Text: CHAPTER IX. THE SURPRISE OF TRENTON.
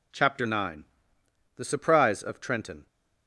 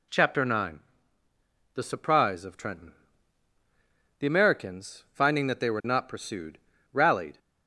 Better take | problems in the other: first | goes on to say "The Americans finding that they were not pursued rallied"; strong; from 4.2 s on; 3.1 s long

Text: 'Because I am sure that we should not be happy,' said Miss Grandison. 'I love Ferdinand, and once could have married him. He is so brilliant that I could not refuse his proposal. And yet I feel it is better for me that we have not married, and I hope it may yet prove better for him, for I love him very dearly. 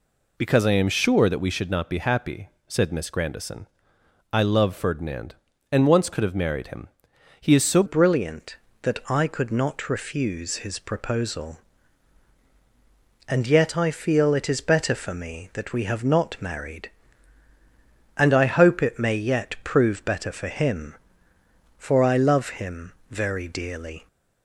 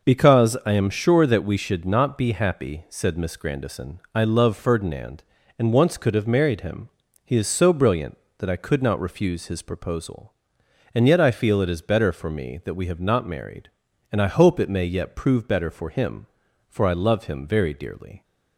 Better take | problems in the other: second | changes voice at "brilliant"; from 7.8 s on; 16.2 s long // pauses between "him" and "very"; slight; at 22.9 s; 0.18 s long

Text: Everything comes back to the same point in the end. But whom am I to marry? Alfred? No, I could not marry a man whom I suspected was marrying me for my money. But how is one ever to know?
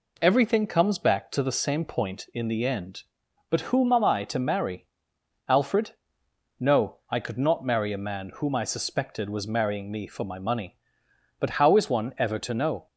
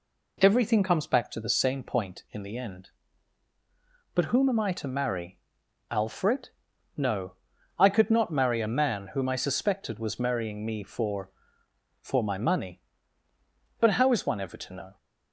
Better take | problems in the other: first | says "for" twice; at 12.0 s

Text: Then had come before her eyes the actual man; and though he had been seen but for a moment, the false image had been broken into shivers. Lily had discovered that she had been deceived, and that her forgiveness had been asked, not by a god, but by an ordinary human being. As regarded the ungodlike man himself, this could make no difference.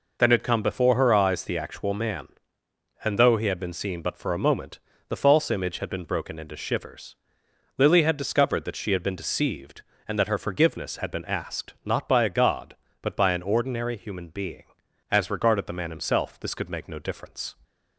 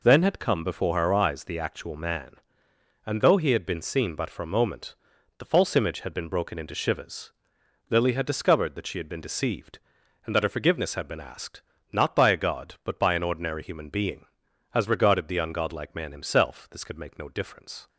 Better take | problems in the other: second | skips "ungodlike"; at 15.7 s

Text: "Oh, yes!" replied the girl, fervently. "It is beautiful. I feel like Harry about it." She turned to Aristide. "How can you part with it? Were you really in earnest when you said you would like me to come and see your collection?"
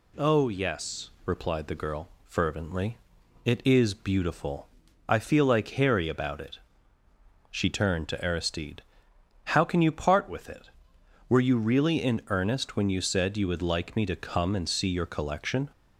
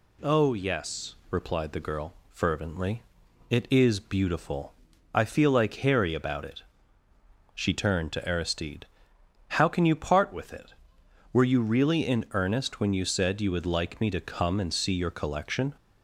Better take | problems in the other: neither | none

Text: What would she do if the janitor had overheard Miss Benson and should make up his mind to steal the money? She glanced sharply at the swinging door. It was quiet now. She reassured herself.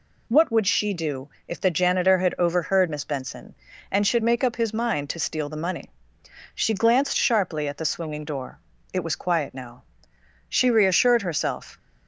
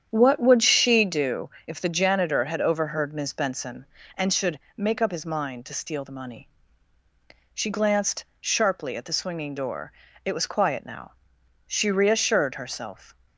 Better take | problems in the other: first | starts louder than the rest; strong; until 1.2 s; 8.5 dB // pauses between "do" and "if"; slight; at 1.5 s; 0.16 s long; slight in the first // pauses between "should" and "make"; slight; at 4.5 s; 0.20 s long // pauses between "glanced" and "sharply"; slight; at 8.2 s; 0.16 s long

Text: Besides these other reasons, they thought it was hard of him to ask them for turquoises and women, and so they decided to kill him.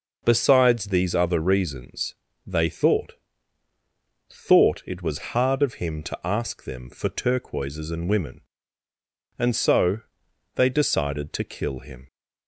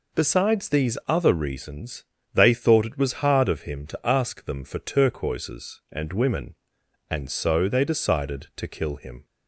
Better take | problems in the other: second | says "thought" twice; at 4.3 s // pauses between "so" and "they"; noticeable; at 9.9 s; 0.56 s long

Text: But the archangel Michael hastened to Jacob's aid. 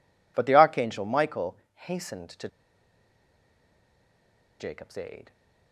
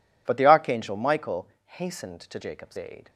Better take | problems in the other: second | pauses between "Michael" and "hastened"; slight; at 1.5 s; 0.20 s long; slight in the second // pauses between "to" and "Jacob's"; strong; at 2.4 s; 2.1 s long

